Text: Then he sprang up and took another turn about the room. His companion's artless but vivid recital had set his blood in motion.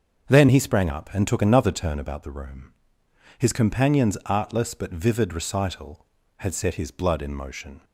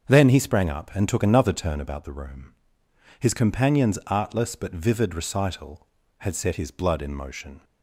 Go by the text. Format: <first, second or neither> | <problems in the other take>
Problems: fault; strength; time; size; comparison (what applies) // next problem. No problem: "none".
neither | starts louder than the rest; the same in both